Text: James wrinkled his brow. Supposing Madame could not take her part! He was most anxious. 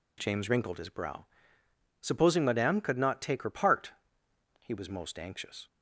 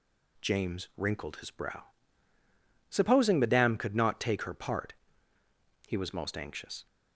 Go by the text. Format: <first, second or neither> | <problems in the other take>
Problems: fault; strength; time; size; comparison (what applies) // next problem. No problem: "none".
neither | none